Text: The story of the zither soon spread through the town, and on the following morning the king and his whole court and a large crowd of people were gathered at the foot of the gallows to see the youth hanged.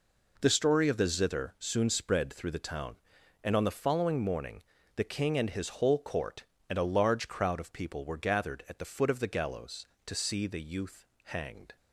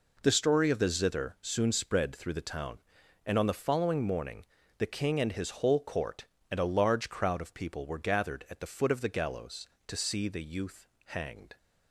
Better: neither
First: pauses between "morning" and "the"; slight; at 4.6 s; 0.34 s long // pauses between "youth" and "hanged"; slight; at 11.0 s; 0.20 s long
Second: pauses between "morning" and "the"; slight; at 4.4 s; 0.34 s long // pauses between "youth" and "hanged"; slight; at 10.8 s; 0.20 s long

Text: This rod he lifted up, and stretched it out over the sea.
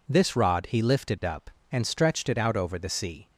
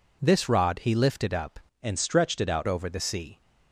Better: first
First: none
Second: changes voice from "and" to "out"; from 1.8 to 2.6 s; 0.8 s long

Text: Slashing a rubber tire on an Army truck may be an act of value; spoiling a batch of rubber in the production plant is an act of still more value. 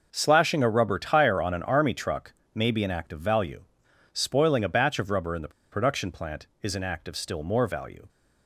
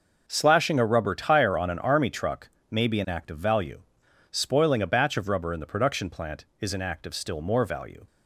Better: second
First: pauses between "truck" and "may"; slight; at 2.3 s; 0.20 s long // pauses between "the" and "production"; slight; at 5.5 s; 0.22 s long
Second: pauses between "truck" and "may"; slight; at 2.4 s; 0.20 s long

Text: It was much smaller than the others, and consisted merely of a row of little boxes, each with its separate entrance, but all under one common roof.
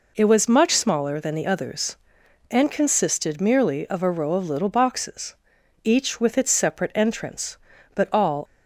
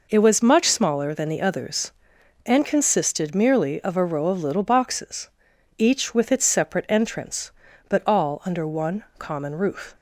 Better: second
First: stops before "under one common roof"; at 8.4 s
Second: none

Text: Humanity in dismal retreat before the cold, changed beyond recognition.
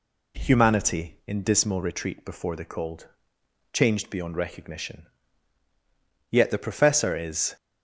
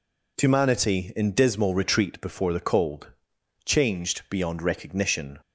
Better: second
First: goes on to say "Yet the Professor is"; noticeable; from 6.2 s on; 1.2 s long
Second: none

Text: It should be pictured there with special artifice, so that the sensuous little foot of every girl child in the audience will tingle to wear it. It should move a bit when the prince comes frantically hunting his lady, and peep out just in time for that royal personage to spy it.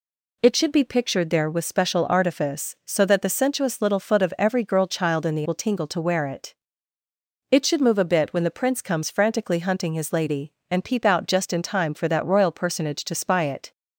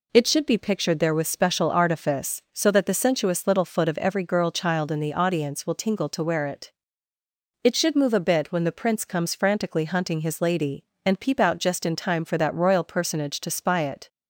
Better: second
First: skips "audience"; at 5.4 s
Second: none

